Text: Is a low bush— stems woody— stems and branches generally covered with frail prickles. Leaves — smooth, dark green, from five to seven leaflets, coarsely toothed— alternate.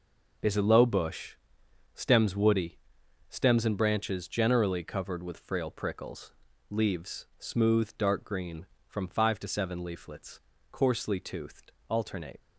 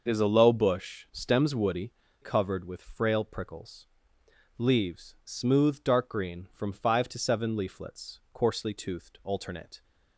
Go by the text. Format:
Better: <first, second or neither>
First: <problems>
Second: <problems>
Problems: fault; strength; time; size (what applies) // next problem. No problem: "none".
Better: first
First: none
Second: starts louder than the rest; noticeable; until 1.0 s; 6 dB // skips "stems and branches generally"; at 2.0 s